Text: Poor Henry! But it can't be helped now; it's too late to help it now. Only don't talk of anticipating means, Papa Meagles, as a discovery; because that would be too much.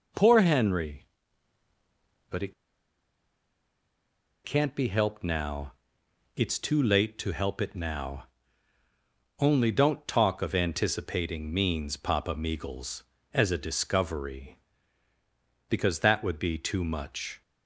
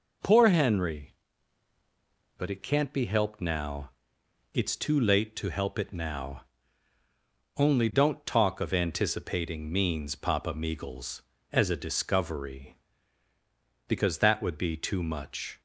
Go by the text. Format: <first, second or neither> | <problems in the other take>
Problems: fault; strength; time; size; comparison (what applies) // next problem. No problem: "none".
second | pauses between "it" and "can't"; strong; at 2.5 s; 1.9 s long